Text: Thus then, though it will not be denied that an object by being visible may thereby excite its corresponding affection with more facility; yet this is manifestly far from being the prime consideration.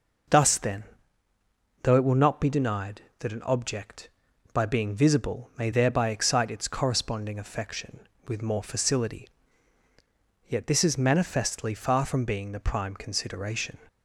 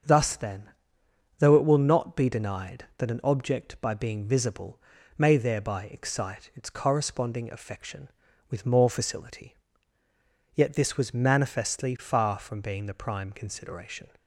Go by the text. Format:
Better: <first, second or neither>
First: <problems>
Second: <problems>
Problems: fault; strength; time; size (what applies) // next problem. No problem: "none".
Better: first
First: none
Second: starts louder than the rest; until 1.7 s; 6.5 dB // pauses between "visible" and "may"; slight; at 4.8 s; 0.36 s long // says "was" for "is"; at 10.9 s